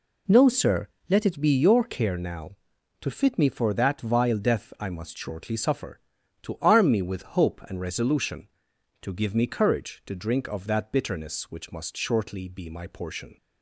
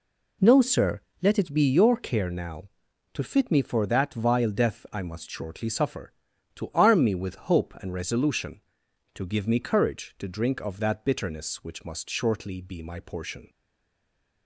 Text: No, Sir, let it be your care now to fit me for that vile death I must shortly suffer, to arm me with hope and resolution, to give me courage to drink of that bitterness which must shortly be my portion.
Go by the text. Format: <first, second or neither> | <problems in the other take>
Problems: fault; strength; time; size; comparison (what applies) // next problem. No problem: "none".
first | stays silent after the last word; from 13.4 s on; 1.0 s long